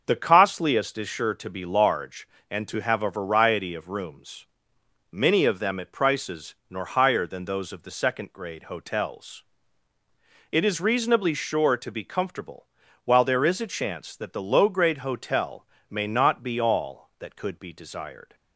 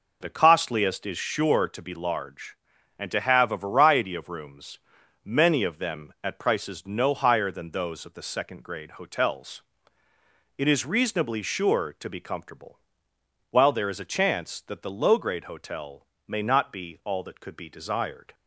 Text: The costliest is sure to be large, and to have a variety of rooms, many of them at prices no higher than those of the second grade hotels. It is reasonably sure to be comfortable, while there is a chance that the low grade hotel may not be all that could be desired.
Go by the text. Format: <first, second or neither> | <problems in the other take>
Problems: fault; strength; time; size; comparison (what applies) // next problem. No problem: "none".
second | starts louder than the rest; until 1.0 s; 6.5 dB // says "nor" for "no"; at 6.6 s // pauses between "hotel" and "may"; slight; at 15.6 s; 0.24 s long; slight in the second